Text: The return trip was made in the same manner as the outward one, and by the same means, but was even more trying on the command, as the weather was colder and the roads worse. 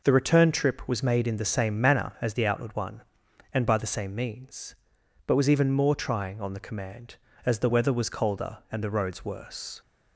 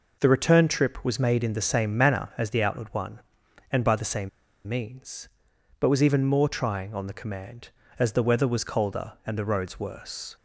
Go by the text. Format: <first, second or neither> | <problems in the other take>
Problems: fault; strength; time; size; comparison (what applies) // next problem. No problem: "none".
first | pauses between "same" and "means"; at 4.2 s; 0.38 s long